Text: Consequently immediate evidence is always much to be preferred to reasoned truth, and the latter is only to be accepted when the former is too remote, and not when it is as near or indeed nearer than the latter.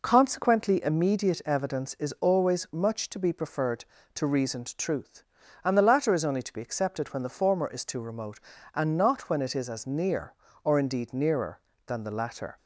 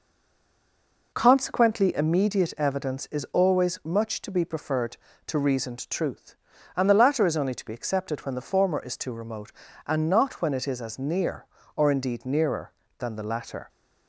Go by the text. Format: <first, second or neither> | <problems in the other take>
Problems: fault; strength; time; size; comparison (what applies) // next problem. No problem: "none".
first | stays silent before the first word; until 1.1 s; 1.1 s long